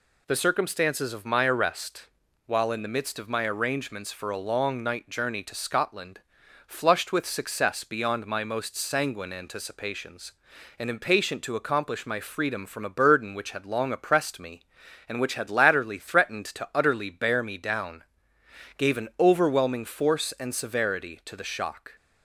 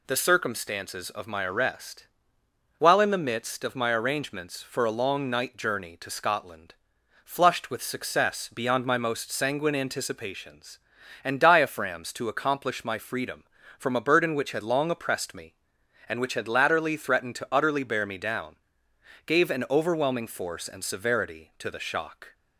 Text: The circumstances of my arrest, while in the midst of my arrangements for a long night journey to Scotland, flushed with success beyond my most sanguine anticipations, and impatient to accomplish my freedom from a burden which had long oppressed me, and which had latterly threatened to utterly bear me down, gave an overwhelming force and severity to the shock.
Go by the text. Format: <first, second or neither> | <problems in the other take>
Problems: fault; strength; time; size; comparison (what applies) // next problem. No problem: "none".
first | says "diaphragms" for "impatient"; at 11.4 s